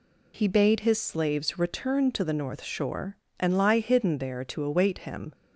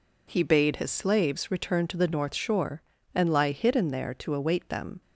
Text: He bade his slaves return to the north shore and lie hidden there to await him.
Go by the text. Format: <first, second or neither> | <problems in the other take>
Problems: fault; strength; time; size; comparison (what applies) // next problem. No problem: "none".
first | says "them" for "him"; at 4.6 s